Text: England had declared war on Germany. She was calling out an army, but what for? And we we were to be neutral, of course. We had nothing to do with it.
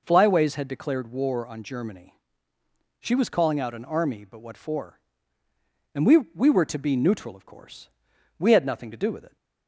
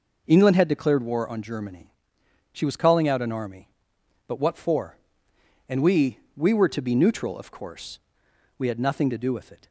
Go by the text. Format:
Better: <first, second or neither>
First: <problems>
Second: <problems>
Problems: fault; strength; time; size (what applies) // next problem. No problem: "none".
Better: second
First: says "Flyways" for "England"; at 0.0 s // pauses between "we" and "we"; slight; at 6.1 s; 0.16 s long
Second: pauses between "we" and "we"; slight; at 6.1 s; 0.18 s long